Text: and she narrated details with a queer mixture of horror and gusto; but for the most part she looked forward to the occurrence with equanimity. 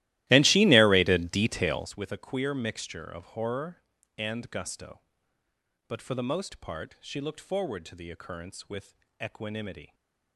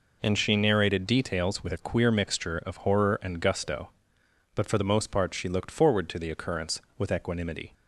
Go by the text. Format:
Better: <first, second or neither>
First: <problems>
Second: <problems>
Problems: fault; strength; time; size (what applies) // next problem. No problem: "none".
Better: second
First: starts louder than the rest; strong; until 2.0 s; 16.5 dB // pauses between "with" and "equanimity"; slight; at 8.9 s; 0.28 s long // stays silent after the last word; slight; from 9.8 s on; 0.5 s long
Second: none